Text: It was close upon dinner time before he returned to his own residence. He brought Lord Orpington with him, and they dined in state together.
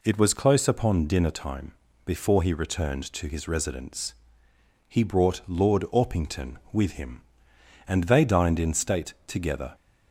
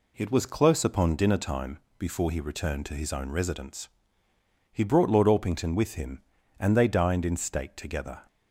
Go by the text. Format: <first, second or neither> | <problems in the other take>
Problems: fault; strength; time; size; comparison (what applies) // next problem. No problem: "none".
second | pauses between "time" and "before"; slight; at 1.7 s; 0.34 s long; slight in the second // skips "own"; at 3.4 s